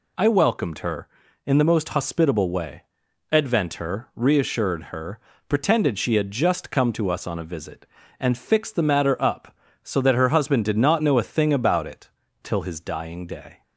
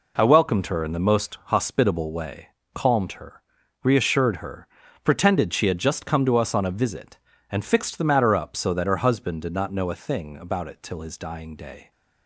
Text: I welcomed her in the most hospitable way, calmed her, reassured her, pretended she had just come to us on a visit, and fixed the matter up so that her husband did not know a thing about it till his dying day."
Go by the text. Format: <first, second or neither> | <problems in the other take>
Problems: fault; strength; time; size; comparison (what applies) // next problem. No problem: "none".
second | says "advent" for "calmed"; at 3.3 s // pauses between "it" and "till"; slight; at 12.0 s; 0.34 s long